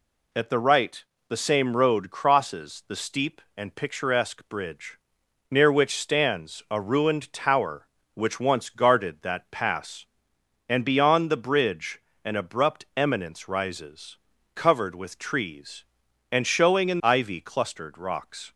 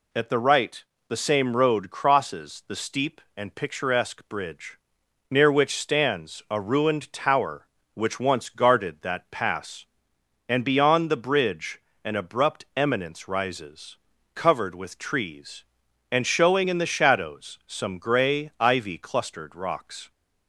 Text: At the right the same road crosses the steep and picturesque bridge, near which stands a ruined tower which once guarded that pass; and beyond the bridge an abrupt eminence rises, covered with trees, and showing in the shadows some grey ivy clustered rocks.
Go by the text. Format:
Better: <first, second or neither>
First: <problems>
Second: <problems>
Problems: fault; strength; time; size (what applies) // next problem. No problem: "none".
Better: second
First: pauses between "right" and "the"; slight; at 1.0 s; 0.24 s long // pauses between "bridge" and "an"; slight; at 11.9 s; 0.24 s long // skips "the shadows some grey"; at 17.0 s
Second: pauses between "right" and "the"; slight; at 0.8 s; 0.24 s long // pauses between "bridge" and "an"; slight; at 11.7 s; 0.24 s long